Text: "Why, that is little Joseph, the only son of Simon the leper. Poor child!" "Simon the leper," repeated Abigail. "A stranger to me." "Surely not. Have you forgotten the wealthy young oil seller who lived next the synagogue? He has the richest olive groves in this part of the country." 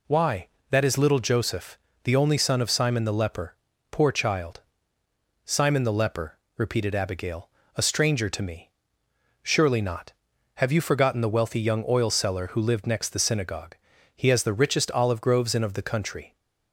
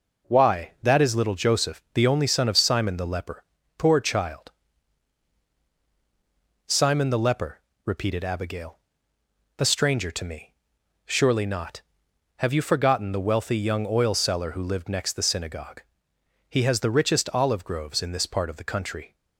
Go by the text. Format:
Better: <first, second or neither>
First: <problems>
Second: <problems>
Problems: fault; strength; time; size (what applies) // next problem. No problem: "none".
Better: second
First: skips "this part"; at 15.6 s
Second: none